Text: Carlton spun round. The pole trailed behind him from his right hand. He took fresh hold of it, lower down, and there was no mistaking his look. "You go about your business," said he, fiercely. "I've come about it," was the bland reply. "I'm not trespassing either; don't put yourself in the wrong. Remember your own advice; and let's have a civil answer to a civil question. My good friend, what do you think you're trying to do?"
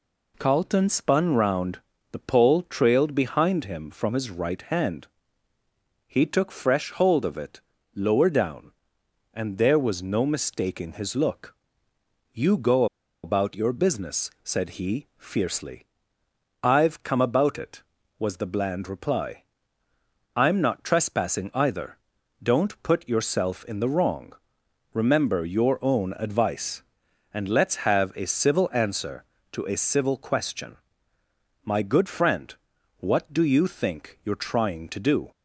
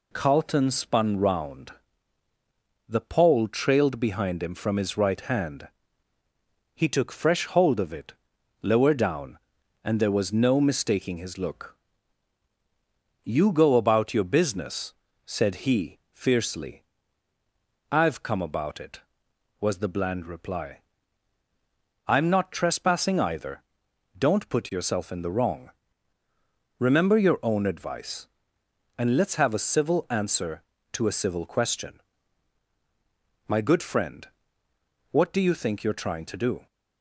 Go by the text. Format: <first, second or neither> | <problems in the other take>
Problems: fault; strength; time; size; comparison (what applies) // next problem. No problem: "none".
second | pauses between "go" and "about"; at 12.8 s; 0.38 s long